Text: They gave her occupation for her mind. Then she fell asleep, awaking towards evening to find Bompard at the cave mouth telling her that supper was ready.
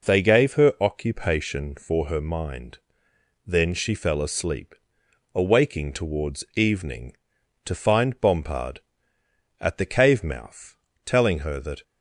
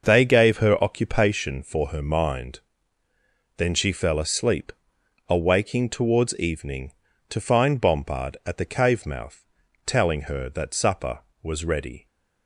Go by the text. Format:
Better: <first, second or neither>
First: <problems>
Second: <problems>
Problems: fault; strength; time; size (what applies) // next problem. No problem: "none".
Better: second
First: pauses between "mouth" and "telling"; slight; at 10.7 s; 0.30 s long // stops before "supper was ready"; at 11.8 s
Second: pauses between "mouth" and "telling"; at 9.4 s; 0.40 s long